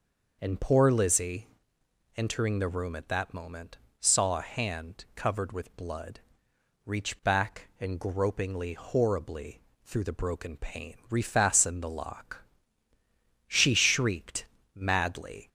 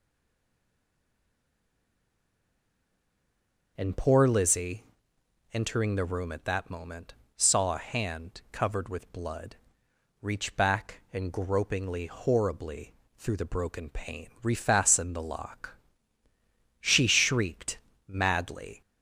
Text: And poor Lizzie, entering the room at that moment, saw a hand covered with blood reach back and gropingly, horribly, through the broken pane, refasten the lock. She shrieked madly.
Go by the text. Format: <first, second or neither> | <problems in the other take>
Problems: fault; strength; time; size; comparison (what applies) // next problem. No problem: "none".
first | stays silent before the first word; strong; until 3.7 s; 3.7 s long // pauses between "blood" and "reach"; noticeable; at 9.5 s; 0.64 s long; noticeable in the first // pauses between "shrieked" and "madly"; slight; at 17.7 s; 0.30 s long; slight in the first